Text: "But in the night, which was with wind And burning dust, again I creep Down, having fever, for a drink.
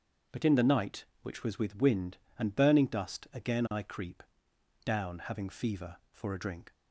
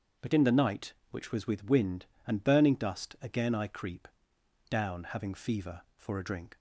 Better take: neither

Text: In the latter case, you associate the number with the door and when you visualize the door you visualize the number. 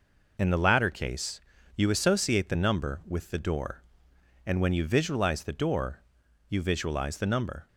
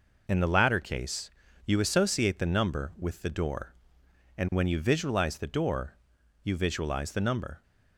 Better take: neither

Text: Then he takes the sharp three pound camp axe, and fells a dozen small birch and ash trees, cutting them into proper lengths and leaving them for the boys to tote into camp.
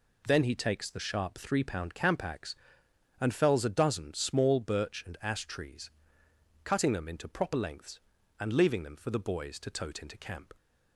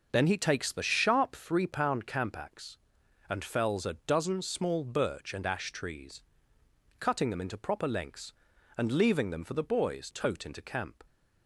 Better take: first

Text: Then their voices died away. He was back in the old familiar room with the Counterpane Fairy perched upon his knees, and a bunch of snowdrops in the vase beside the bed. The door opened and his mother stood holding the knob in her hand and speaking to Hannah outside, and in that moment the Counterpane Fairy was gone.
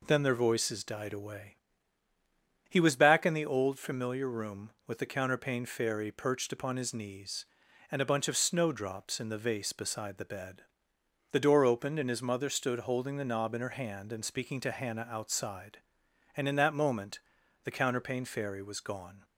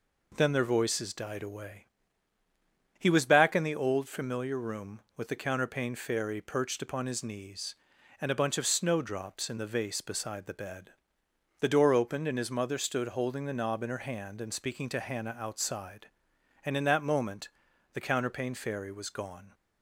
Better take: neither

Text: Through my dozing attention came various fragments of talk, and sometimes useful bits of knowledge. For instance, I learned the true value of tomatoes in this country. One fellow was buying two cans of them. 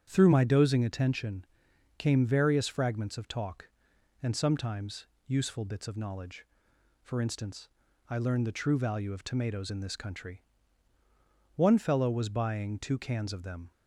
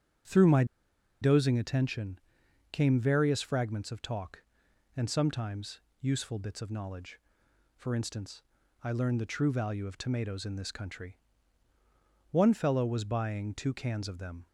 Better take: first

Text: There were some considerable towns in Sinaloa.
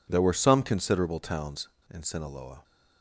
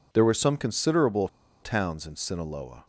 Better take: first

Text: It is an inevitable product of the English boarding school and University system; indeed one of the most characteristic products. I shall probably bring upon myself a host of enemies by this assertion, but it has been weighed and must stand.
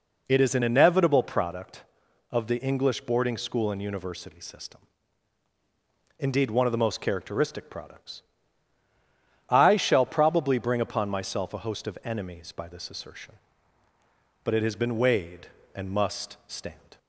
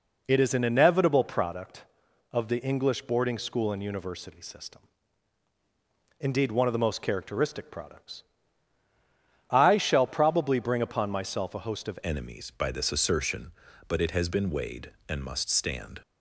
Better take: first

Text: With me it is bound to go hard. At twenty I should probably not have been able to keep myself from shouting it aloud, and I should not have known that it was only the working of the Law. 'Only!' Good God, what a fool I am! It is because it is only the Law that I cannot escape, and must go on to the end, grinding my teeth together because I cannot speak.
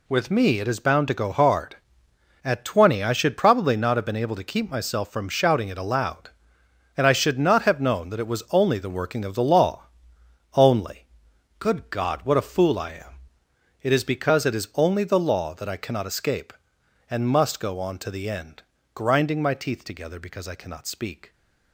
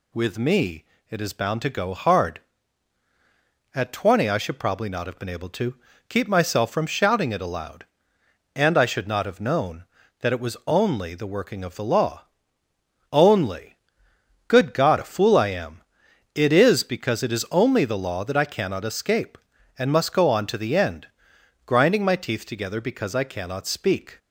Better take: first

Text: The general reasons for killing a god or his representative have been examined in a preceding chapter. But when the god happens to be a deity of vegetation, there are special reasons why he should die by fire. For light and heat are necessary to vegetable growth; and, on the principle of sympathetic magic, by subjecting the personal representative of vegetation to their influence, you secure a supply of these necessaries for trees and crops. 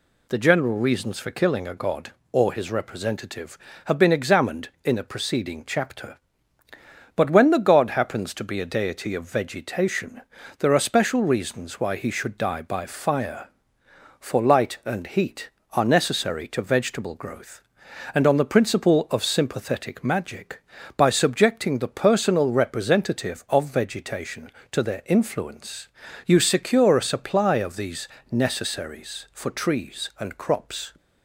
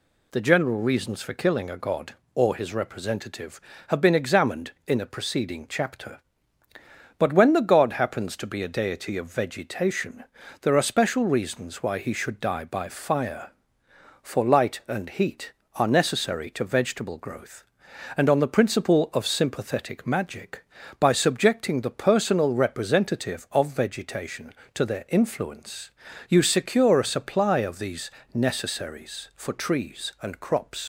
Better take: first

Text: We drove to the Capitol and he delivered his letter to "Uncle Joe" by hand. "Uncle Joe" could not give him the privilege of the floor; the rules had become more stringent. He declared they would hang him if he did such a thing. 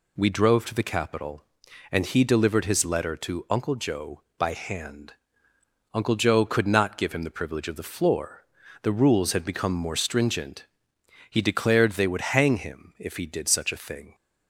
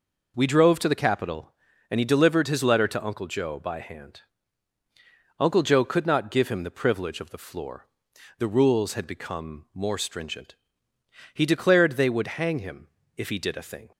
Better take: first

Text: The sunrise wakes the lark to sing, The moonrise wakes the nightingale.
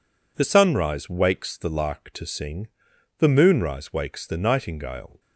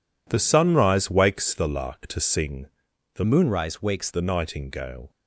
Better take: first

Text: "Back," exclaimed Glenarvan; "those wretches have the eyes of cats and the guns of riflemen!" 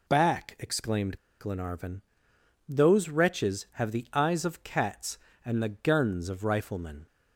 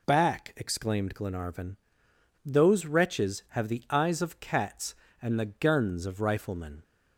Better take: second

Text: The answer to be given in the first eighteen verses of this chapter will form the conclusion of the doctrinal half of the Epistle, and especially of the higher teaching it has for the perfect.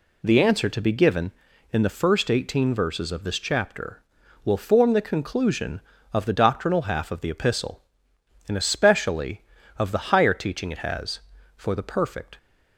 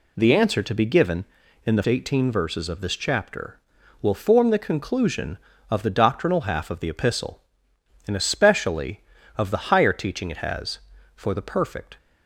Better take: first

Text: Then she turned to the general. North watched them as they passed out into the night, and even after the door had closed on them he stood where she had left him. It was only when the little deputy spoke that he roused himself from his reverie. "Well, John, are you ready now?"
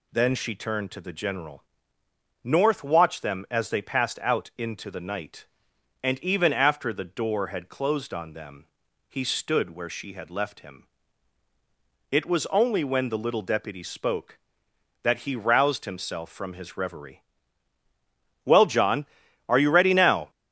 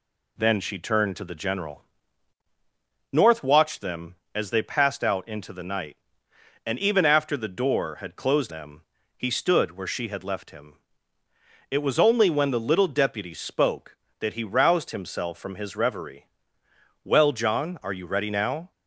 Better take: first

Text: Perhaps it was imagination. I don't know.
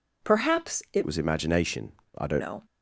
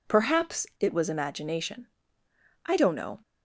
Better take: second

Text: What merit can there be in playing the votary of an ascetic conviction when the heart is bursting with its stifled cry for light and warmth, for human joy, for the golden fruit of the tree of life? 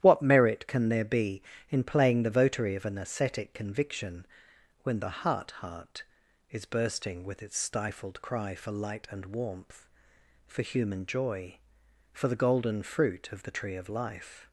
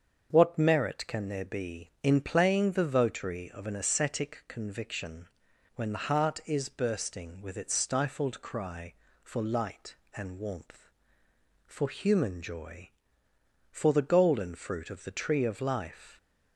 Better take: second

